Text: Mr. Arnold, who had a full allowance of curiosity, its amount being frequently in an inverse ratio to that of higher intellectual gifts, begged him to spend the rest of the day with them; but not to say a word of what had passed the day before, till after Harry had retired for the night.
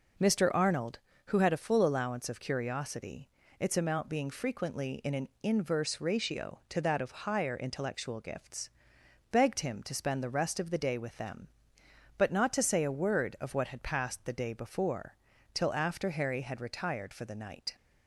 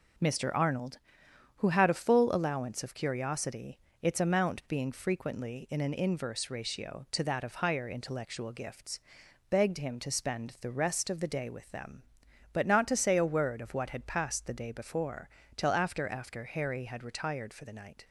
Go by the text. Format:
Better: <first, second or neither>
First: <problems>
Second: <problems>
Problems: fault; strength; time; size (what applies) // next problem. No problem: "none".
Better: first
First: none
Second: says "after" twice; at 16.0 s